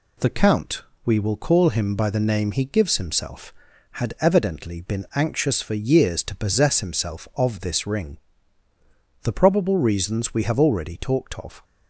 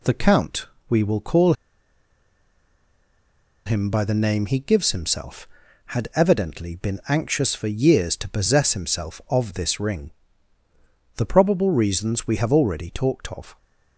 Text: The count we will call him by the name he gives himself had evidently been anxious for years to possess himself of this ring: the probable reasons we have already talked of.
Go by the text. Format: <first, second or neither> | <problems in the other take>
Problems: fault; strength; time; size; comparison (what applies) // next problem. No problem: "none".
first | pauses between "count" and "we"; slight; at 0.6 s; 0.22 s long; slight in the first // pauses between "call" and "him"; strong; at 1.5 s; 2.1 s long